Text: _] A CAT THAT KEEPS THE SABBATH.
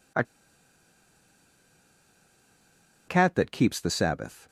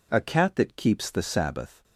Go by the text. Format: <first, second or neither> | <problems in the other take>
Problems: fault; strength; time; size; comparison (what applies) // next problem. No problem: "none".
second | pauses between "A" and "CAT"; strong; at 0.2 s; 2.8 s long